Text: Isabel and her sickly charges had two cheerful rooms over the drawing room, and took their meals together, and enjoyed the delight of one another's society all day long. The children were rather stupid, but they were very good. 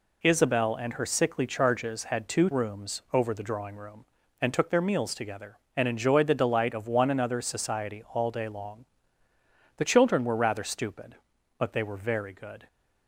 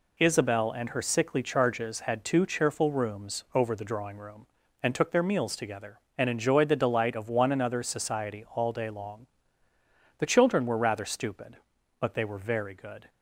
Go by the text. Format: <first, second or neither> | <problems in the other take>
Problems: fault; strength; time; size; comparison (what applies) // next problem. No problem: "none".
second | skips "cheerful"; at 2.5 s